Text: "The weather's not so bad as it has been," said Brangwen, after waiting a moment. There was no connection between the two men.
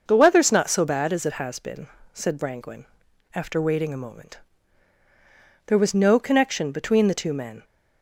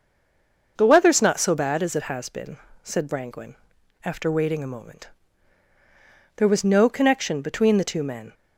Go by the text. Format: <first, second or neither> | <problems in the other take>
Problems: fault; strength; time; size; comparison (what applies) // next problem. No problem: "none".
first | stays silent before the first word; slight; until 0.7 s; 0.7 s long // starts louder than the rest; noticeable; until 1.7 s; 6 dB; noticeable in the first